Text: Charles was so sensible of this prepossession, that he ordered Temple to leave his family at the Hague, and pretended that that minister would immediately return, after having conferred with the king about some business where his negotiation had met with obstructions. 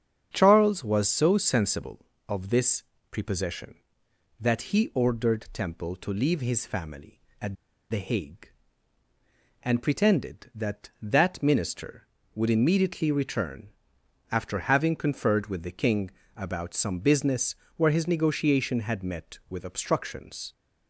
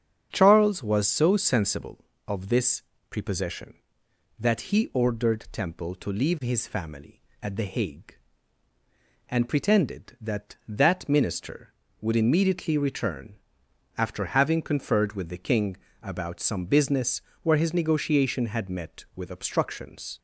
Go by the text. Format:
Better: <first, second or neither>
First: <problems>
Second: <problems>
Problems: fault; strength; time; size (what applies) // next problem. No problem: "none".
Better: second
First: starts louder than the rest; strong; until 1.3 s; 8 dB // pauses between "this" and "prepossession"; slight; at 2.8 s; 0.28 s long // pauses between "at" and "the"; slight; at 7.5 s; 0.35 s long // pauses between "king" and "about"; slight; at 16.1 s; 0.26 s long // pauses between "business" and "where"; slight; at 17.5 s; 0.22 s long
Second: starts louder than the rest; strong; until 1.3 s; 8 dB // pauses between "this" and "prepossession"; slight; at 2.8 s; 0.28 s long // pauses between "king" and "about"; slight; at 15.7 s; 0.26 s long // pauses between "business" and "where"; slight; at 17.2 s; 0.22 s long